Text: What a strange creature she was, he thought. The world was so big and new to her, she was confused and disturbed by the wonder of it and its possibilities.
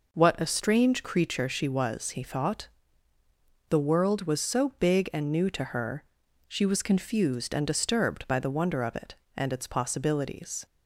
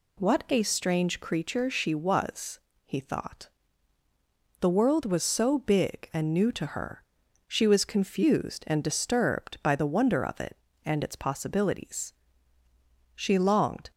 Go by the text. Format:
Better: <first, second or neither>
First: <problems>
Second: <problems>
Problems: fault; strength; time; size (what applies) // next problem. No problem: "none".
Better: first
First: none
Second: goes on to say "She longed"; noticeable; from 13.1 s on; 0.76 s long